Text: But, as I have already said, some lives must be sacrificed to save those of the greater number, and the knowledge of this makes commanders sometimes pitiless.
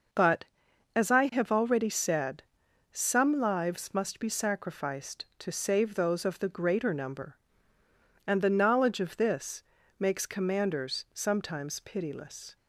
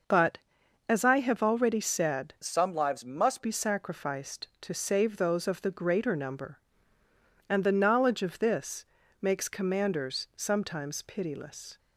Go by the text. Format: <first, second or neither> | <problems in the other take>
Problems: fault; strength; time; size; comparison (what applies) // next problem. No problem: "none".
first | changes voice from "some" to "must"; from 2.4 to 3.4 s; 1.0 s long // pauses between "this" and "makes"; slight; at 8.8 s; 0.34 s long; slight in the first